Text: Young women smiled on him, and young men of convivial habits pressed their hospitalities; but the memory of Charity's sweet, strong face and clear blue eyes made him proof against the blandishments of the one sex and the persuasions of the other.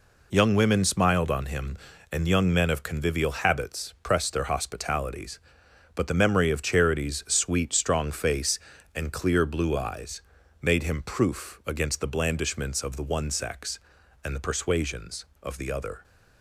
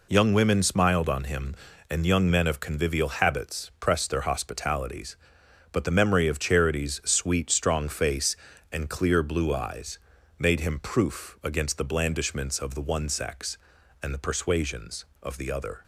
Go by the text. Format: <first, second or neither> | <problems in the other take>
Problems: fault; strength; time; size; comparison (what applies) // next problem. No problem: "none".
neither | pauses between "eyes" and "made"; the same in both